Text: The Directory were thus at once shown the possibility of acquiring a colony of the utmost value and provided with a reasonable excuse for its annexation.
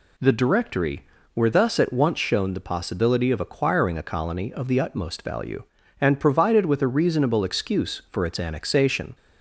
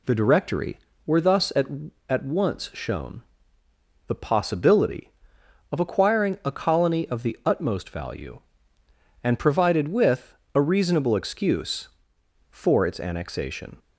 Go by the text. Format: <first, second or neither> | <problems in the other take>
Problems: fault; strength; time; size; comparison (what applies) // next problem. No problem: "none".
first | says "at" twice; at 2.0 s // pauses between "shown" and "the"; noticeable; at 3.2 s; 0.86 s long // pauses between "with" and "a"; slight; at 10.3 s; 0.20 s long